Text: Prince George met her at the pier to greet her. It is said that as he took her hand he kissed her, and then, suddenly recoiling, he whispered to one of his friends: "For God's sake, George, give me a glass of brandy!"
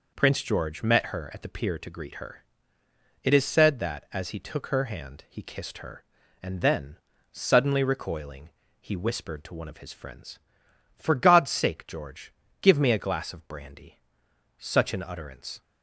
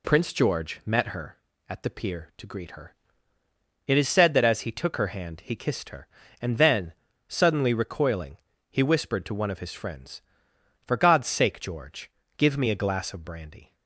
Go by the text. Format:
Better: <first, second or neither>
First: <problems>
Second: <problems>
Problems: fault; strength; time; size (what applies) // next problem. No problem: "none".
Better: second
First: goes on to say "Such an utterance"; noticeable; from 14.5 s on; 1.0 s long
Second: none